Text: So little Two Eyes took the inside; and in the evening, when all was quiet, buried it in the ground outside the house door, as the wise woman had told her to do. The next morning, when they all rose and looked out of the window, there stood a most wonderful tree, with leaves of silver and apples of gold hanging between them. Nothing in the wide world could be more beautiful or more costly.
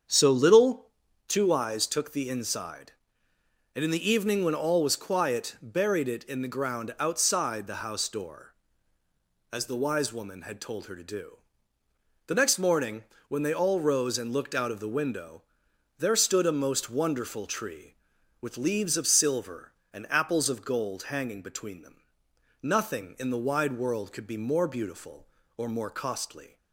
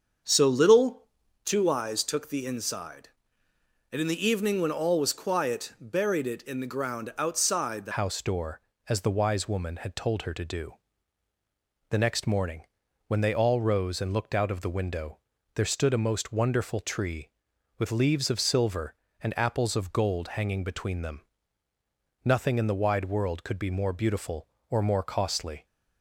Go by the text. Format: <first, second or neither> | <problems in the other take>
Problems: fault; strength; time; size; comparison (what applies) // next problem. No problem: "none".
first | starts louder than the rest; until 1.6 s; 7 dB; strong in the first // pauses between "little" and "Two"; at 1.0 s; 0.40 s long; also in the first // changes voice at "house"; from 7.9 s on; 17.7 s long